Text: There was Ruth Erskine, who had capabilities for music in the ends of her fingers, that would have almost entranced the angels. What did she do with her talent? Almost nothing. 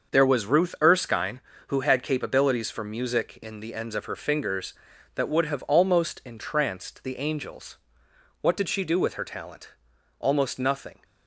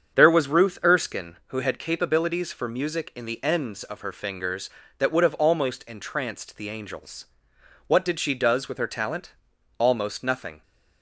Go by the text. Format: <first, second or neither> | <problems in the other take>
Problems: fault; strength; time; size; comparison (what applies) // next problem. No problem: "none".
first | starts louder than the rest; strong; until 1.2 s; 7.5 dB; also in the first // says "does" for "do"; at 8.3 s